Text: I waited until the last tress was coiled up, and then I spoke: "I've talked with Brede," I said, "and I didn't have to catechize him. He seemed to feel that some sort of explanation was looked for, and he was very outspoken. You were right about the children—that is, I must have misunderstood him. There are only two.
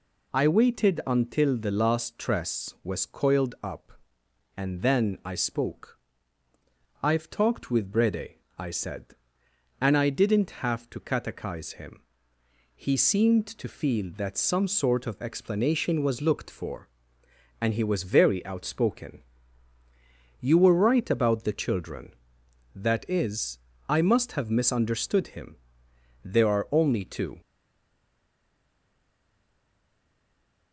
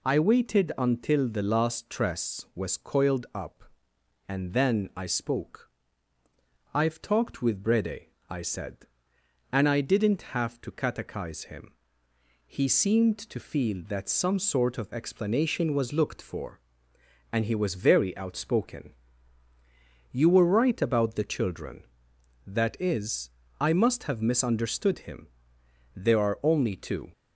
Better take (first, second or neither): second